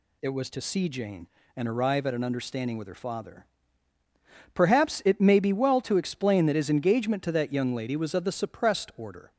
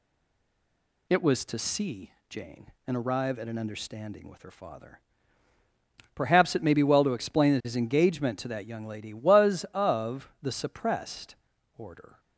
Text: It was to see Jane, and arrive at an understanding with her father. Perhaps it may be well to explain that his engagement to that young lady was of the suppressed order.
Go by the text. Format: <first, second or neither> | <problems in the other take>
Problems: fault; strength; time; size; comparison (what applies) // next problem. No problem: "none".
first | stays silent before the first word; until 1.0 s; 1.0 s long // pauses between "see" and "Jane"; slight; at 2.1 s; 0.18 s long // pauses between "suppressed" and "order"; at 11.3 s; 0.42 s long